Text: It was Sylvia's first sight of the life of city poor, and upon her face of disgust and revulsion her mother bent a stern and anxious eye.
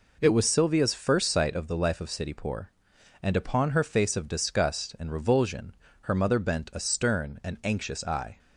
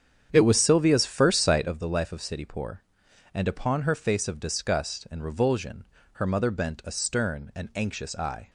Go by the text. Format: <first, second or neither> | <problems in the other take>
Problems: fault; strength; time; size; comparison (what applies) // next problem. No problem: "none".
first | starts louder than the rest; strong; until 1.9 s; 8.5 dB // pauses between "revulsion" and "her"; slight; at 5.8 s; 0.28 s long; slight in the first